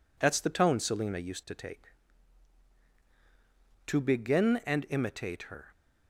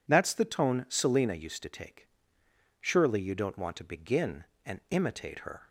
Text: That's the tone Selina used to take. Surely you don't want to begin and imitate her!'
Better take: second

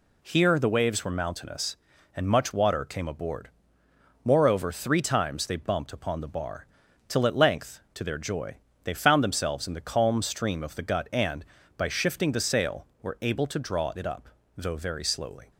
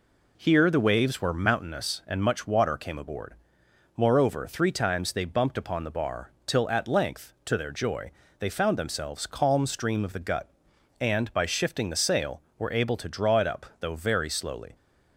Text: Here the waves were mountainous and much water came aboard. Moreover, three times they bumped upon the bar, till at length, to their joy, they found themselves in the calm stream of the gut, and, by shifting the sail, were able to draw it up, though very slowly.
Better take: first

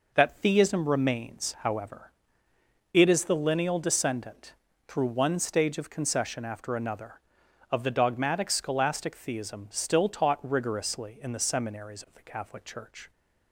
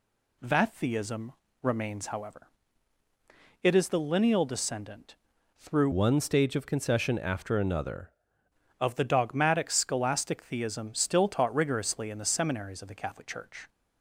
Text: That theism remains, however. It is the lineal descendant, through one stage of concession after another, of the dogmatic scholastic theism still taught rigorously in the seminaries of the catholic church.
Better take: first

